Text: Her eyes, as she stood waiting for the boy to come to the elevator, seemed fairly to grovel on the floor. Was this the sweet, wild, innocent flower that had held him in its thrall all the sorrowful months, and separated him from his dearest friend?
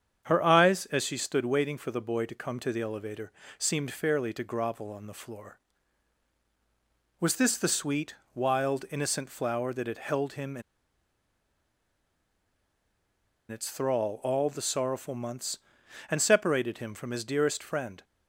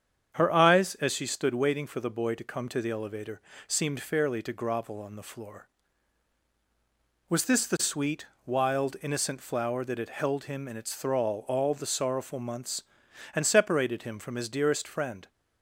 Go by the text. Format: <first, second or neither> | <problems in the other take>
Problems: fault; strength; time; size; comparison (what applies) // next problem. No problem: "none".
second | starts louder than the rest; strong; until 1.2 s; 8 dB; strong in the second // pauses between "in" and "its"; strong; at 10.6 s; 2.8 s long